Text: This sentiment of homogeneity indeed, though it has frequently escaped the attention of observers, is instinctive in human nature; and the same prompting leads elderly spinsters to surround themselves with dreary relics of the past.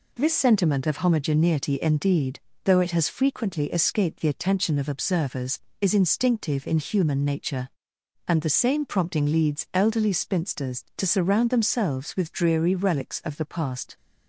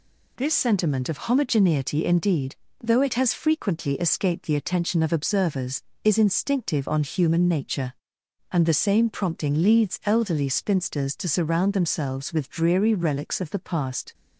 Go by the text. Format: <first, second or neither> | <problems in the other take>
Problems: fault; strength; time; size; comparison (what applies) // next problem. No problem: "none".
first | says "on" for "in"; at 6.8 s